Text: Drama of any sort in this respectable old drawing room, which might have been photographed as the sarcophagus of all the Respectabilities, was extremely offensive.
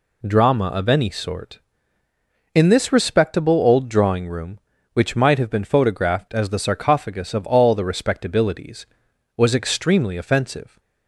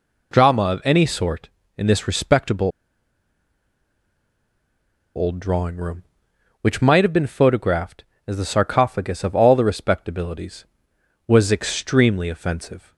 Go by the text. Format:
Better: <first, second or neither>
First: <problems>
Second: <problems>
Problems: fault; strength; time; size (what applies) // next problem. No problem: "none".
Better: first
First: none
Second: pauses between "respectable" and "old"; strong; at 2.6 s; 2.4 s long